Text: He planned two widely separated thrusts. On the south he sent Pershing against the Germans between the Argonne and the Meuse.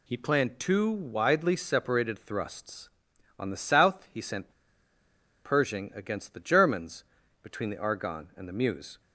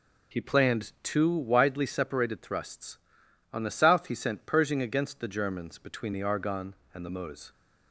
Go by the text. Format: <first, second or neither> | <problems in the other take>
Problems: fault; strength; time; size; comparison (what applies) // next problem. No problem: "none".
second | pauses between "sent" and "Pershing"; noticeable; at 4.5 s; 0.93 s long // pauses between "Germans" and "between"; slight; at 7.0 s; 0.36 s long